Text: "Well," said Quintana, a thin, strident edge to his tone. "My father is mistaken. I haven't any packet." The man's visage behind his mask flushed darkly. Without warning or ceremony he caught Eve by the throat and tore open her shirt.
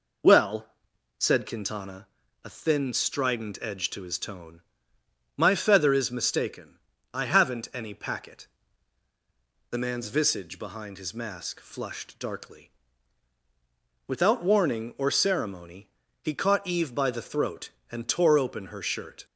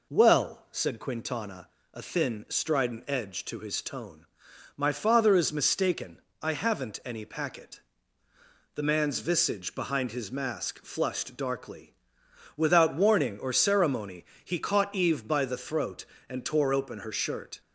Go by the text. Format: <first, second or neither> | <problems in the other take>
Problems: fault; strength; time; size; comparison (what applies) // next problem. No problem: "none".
second | says "feather" for "father"; at 5.5 s // pauses between "ceremony" and "he"; slight; at 15.8 s; 0.34 s long; slight in the second